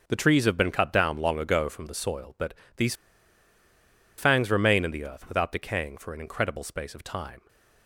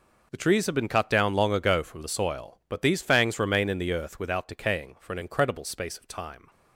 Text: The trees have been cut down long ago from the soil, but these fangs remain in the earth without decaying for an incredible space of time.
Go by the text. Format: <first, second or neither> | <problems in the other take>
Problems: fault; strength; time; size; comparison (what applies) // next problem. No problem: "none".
second | pauses between "but" and "these"; slight; at 2.5 s; 0.22 s long // pauses between "these" and "fangs"; at 2.9 s; 1.2 s long